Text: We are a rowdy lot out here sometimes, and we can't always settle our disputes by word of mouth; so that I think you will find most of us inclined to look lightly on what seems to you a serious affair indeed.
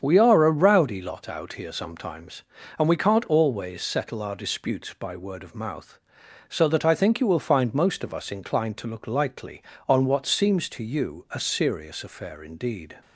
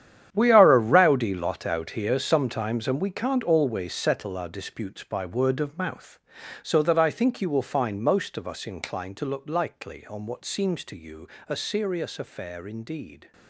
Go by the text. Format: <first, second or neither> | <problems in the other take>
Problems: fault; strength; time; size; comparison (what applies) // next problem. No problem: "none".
first | gets quieter; strong; throughout; 13.5 dB // starts louder than the rest; strong; until 1.3 s; 10 dB; strong in the first // pauses between "you" and "a"; slight; at 11.2 s; 0.22 s long